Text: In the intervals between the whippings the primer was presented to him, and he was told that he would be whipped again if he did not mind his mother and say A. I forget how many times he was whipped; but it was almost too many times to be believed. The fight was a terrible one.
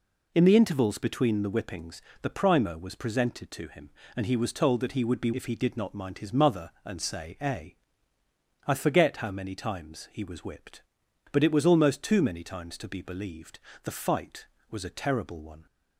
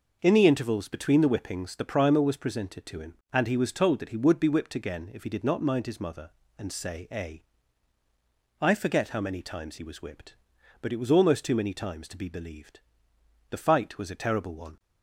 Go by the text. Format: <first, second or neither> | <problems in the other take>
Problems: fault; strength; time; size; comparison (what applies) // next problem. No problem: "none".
second | pauses between "whippings" and "the"; slight; at 2.0 s; 0.20 s long // skips "whipped again"; at 5.3 s